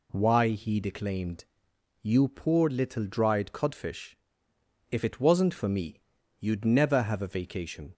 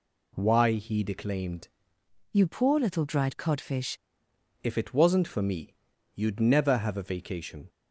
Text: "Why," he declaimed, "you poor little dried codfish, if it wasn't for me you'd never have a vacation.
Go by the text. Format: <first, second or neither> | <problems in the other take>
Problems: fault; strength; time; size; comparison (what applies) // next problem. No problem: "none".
first | changes voice from "you" to "codfish"; from 2.3 to 3.9 s; 1.6 s long // pauses between "me" and "you'd"; at 5.7 s; 0.42 s long; also in the first